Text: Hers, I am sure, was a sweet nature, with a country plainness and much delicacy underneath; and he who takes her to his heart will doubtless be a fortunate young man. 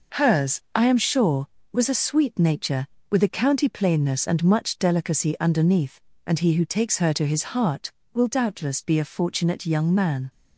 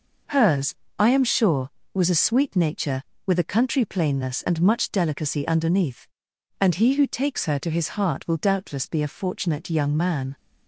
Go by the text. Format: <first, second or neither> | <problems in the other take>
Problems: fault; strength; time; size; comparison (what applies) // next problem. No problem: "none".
second | says "county" for "country"; at 3.2 s